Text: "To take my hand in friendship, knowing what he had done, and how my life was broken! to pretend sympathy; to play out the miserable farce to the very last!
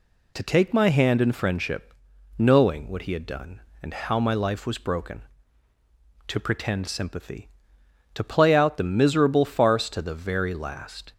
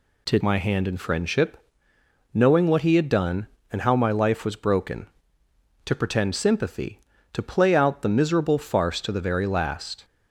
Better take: first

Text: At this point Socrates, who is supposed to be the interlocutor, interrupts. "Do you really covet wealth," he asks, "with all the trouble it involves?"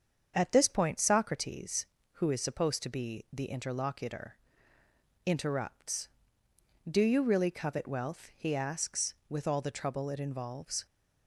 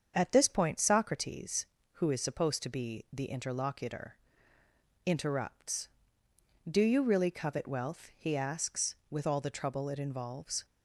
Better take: neither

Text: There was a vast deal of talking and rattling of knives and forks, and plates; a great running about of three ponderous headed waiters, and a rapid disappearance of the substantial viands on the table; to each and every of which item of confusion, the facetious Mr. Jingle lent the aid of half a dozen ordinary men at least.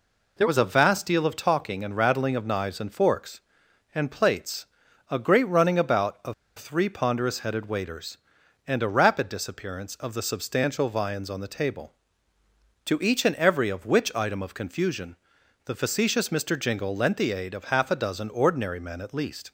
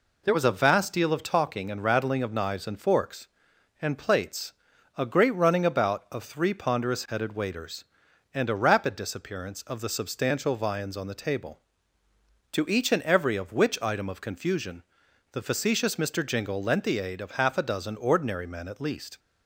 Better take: second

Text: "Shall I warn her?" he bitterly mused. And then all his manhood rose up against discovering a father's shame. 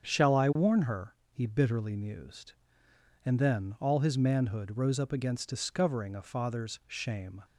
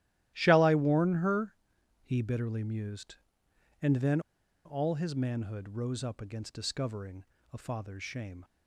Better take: first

